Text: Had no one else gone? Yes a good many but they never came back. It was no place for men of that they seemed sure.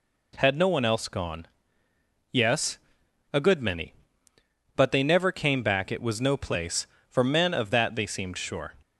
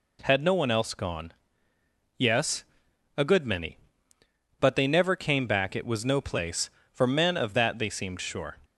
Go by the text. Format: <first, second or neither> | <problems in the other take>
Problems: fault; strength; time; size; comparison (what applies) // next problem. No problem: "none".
neither | pauses between "Yes" and "a"; noticeable; the same in both